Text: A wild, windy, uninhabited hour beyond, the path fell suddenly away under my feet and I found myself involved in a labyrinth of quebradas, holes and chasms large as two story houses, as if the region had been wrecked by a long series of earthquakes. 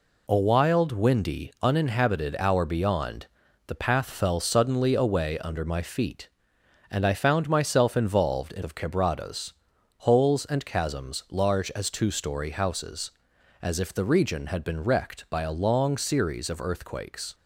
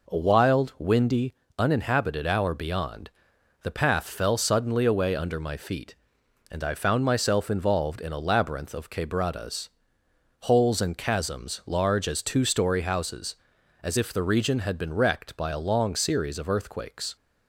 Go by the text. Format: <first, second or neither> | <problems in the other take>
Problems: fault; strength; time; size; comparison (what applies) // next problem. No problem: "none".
second | skips "a labyrinth"; at 8.6 s